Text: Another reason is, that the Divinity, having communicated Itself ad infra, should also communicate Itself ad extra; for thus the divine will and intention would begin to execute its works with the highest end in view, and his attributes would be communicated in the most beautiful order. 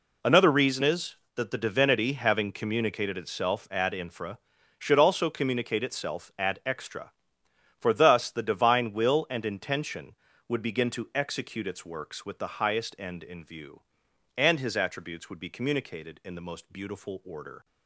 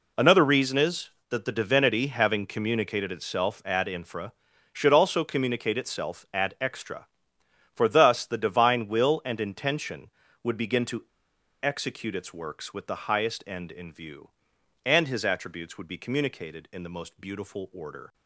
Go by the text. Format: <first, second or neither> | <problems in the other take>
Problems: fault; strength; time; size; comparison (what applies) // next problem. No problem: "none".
first | pauses between "to" and "execute"; noticeable; at 11.0 s; 0.59 s long